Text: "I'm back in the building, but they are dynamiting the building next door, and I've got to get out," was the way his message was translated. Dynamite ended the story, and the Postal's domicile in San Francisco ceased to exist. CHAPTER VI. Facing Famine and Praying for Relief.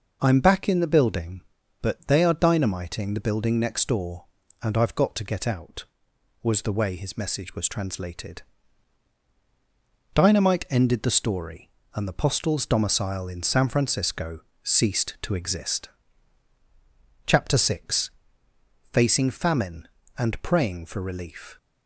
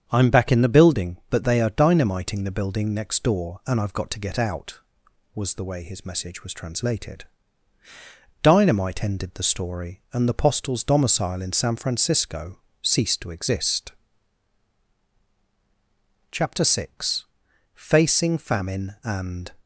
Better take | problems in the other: first | starts louder than the rest; strong; until 1.0 s; 7.5 dB // pauses between "Francisco" and "ceased"; slight; at 12.6 s; 0.22 s long; slight in the first // stops before "Praying for Relief"; at 19.6 s

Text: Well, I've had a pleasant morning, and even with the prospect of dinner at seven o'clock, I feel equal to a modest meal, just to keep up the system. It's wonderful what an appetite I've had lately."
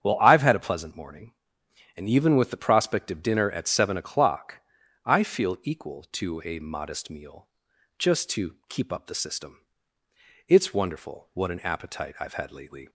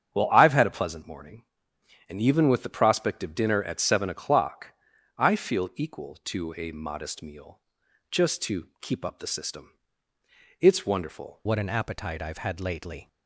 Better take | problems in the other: first | starts louder than the rest; strong; until 1.1 s; 7.5 dB; strong in the first // changes voice at "what"; from 11.4 s on; 1.6 s long

